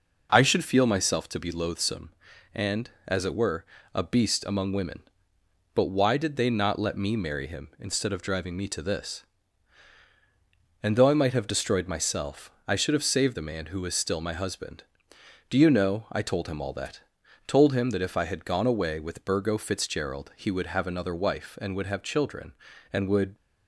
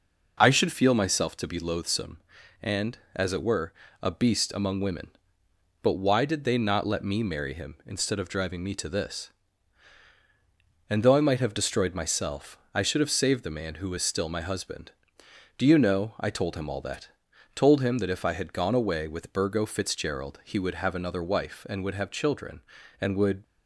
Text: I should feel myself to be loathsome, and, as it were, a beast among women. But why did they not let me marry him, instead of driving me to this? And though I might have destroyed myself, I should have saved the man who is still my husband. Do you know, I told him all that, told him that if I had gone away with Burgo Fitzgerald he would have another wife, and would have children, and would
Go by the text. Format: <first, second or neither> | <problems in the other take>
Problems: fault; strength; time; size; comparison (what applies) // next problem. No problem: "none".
neither | none